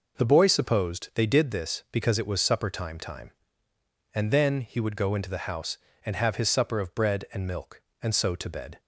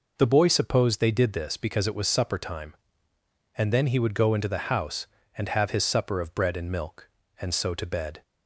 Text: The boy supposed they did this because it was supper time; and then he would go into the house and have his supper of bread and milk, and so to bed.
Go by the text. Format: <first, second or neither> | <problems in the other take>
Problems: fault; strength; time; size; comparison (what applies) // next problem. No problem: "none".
second | says "time" twice; at 2.9 s